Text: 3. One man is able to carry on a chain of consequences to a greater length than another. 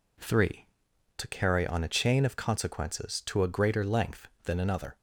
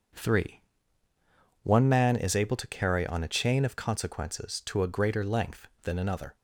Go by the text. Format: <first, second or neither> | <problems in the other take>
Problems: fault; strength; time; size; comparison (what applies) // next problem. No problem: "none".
second | skips "One man is able"; at 0.9 s